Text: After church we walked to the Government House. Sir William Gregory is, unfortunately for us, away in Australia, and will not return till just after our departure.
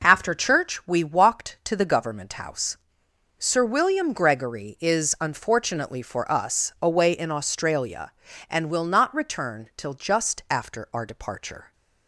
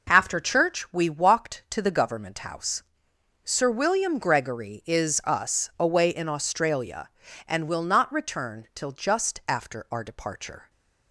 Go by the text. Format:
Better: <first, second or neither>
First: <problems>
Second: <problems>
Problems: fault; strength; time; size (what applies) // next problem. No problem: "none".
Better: first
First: none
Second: skips "unfortunately for"; at 5.2 s